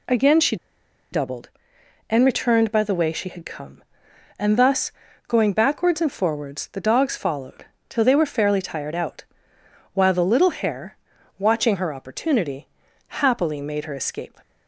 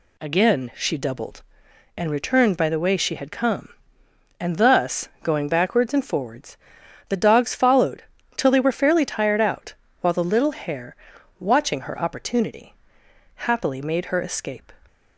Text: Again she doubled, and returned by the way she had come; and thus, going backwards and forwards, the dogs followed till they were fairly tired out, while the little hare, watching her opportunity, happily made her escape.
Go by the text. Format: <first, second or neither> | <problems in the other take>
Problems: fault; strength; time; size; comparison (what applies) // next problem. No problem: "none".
second | pauses between "she" and "doubled"; noticeable; at 0.5 s; 0.56 s long // pauses between "followed" and "till"; slight; at 7.6 s; 0.24 s long; slight in the second